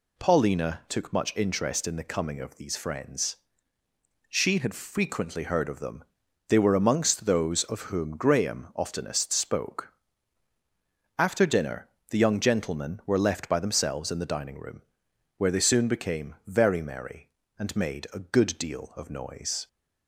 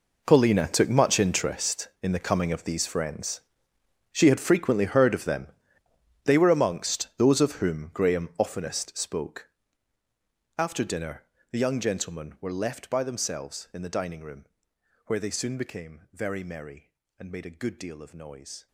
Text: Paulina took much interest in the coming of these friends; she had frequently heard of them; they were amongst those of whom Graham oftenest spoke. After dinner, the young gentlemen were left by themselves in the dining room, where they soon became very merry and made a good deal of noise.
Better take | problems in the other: first | gets quieter; strong; throughout; 17 dB

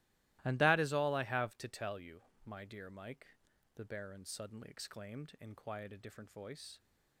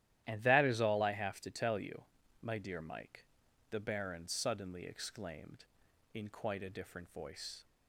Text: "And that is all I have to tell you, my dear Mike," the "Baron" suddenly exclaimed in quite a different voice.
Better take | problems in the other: second | starts louder than the rest; strong; until 1.4 s; 17 dB; strong in the second // says "quiet" for "quite"; at 5.5 s

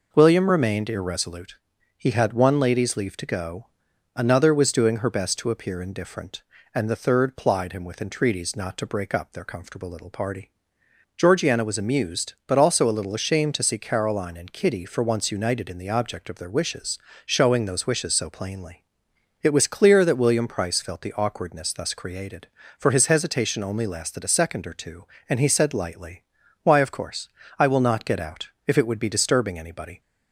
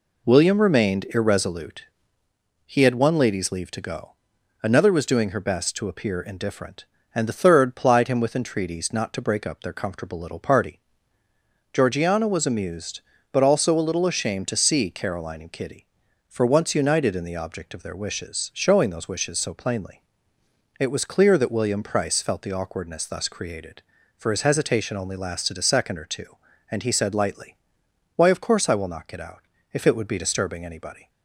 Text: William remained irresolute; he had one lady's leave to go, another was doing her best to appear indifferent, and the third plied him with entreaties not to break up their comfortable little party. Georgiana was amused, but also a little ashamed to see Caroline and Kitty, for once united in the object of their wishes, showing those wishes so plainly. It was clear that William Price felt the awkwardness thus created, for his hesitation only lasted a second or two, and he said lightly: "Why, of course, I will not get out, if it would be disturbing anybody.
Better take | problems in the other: neither | none

